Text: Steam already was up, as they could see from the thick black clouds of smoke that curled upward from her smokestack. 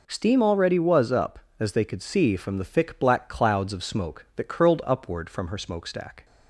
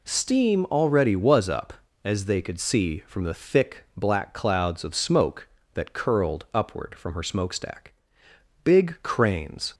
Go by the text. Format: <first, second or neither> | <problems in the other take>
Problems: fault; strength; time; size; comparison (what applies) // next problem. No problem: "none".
first | goes on to say "Big cranes"; noticeable; from 8.6 s on; 1.1 s long